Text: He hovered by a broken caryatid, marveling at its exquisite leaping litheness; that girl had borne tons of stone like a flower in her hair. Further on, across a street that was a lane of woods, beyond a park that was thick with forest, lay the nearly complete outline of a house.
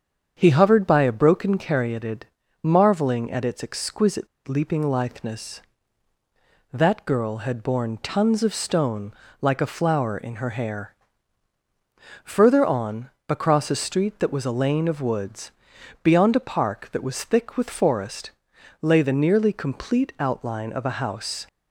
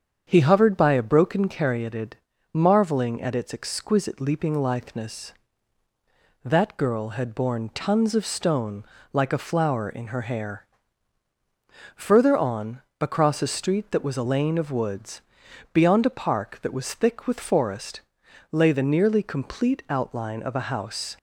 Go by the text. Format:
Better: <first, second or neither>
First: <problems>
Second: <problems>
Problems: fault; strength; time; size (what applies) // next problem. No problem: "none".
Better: second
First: starts louder than the rest; strong; until 1.3 s; 7.5 dB // pauses between "exquisite" and "leaping"; slight; at 4.2 s; 0.19 s long // pauses between "stone" and "like"; slight; at 9.1 s; 0.30 s long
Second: starts louder than the rest; strong; until 1.2 s; 7.5 dB // pauses between "stone" and "like"; slight; at 8.8 s; 0.30 s long